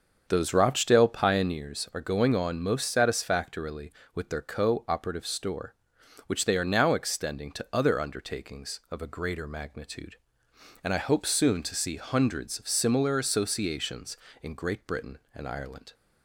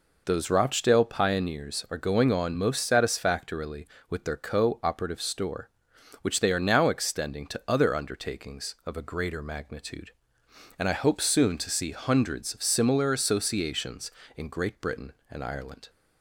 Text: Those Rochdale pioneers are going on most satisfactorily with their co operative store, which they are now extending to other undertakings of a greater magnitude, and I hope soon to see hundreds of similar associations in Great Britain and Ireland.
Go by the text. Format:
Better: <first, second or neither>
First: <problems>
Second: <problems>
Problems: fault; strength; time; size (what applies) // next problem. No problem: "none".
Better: second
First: starts louder than the rest; until 1.7 s; 7 dB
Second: none